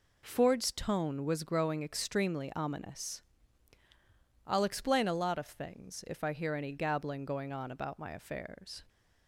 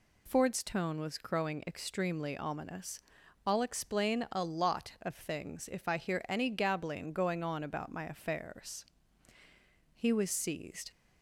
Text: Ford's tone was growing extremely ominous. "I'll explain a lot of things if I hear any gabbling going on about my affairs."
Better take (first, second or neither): first